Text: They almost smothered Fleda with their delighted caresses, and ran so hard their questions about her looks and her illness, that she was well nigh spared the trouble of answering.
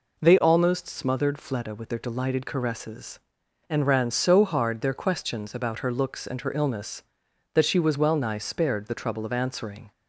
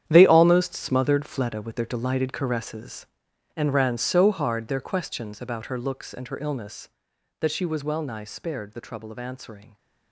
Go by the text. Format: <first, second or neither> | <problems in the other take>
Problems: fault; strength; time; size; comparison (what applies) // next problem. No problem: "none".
first | gets quieter; strong; throughout; 12.5 dB